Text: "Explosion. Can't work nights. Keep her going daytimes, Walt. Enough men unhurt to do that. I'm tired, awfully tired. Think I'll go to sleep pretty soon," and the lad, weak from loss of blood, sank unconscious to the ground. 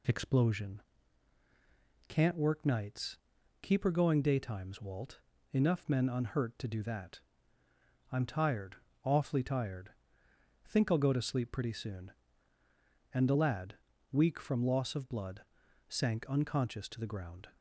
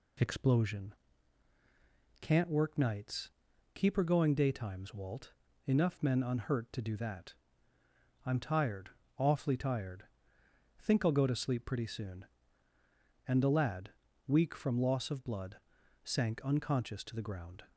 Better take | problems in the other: neither | none

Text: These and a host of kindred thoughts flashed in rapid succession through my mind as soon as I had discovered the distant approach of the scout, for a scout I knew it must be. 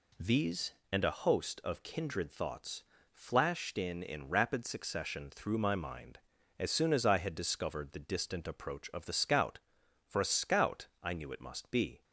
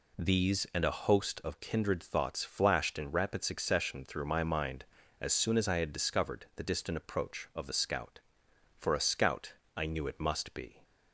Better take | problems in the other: second | pauses between "thoughts" and "flashed"; slight; at 2.8 s; 0.28 s long // says "in" twice; at 4.0 s // pauses between "scout" and "I"; slight; at 10.8 s; 0.16 s long; slight in the second

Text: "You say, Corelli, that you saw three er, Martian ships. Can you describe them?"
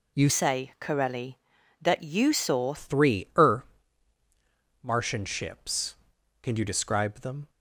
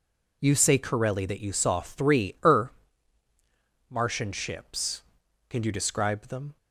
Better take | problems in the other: second | changes voice from "say" to "saw"; from 0.2 to 2.7 s; 2.5 s long

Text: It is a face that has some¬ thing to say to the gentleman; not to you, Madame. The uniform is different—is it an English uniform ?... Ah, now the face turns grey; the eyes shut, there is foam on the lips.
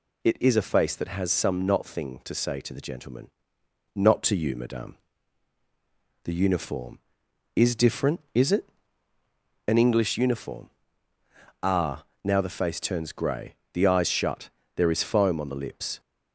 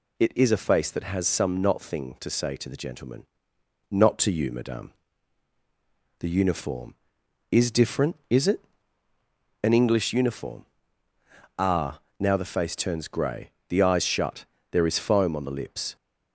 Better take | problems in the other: neither | pauses between "it" and "an"; the same in both

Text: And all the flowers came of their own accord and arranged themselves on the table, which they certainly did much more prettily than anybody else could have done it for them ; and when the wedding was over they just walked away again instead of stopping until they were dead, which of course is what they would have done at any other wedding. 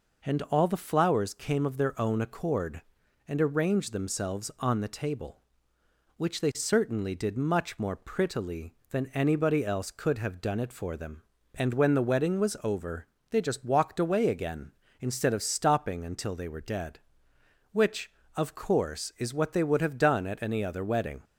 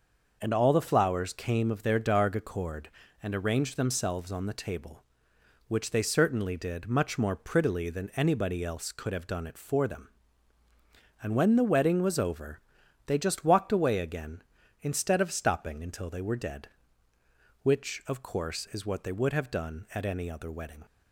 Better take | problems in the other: first | starts louder than the rest; noticeable; until 1.4 s; 6 dB // says "darg" for "own"; at 1.9 s // pauses between "over" and "they"; noticeable; at 12.5 s; 0.46 s long; slight in the first

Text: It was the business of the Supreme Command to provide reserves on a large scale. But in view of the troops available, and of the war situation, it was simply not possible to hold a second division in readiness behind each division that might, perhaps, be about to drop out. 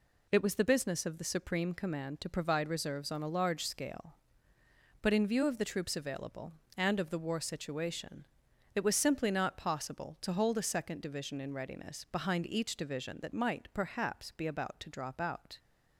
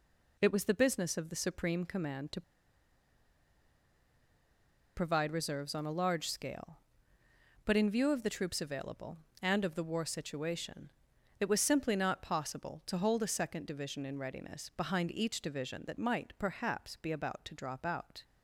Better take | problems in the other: first | pauses between "to" and "provide"; strong; at 2.4 s; 2.5 s long

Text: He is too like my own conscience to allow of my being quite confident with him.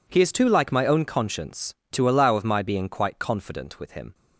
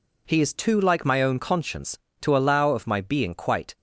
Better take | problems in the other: first | stops before "confident with him"; at 3.7 s

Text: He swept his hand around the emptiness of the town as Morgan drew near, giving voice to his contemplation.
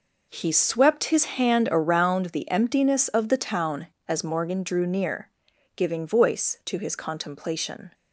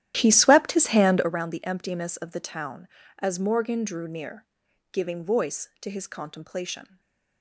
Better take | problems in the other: first | starts louder than the rest; strong; until 1.4 s; 12.5 dB // stays silent after the last word; slight; from 6.8 s on; 0.6 s long

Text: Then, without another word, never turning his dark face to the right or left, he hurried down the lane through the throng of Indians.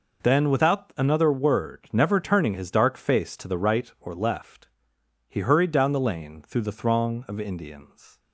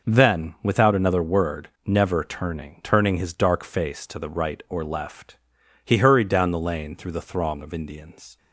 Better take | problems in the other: first | says "turning" twice; at 2.8 s

